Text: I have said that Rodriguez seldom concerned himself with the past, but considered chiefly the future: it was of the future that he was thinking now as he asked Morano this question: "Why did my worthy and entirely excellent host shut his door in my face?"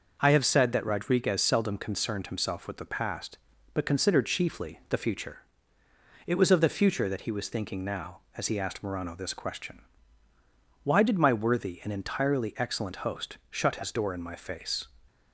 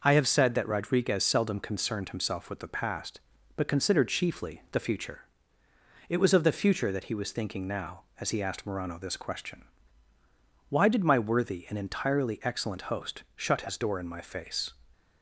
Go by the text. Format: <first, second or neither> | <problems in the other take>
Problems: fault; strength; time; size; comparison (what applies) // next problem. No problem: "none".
neither | none